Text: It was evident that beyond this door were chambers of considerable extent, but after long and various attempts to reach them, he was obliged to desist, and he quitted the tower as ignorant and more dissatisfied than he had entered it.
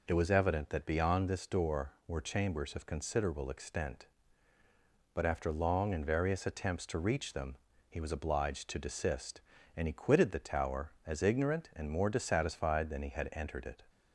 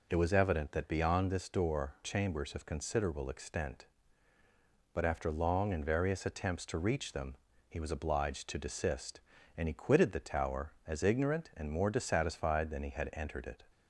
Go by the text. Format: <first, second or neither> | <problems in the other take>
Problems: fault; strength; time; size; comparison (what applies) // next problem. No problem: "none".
first | skips "were"; at 1.9 s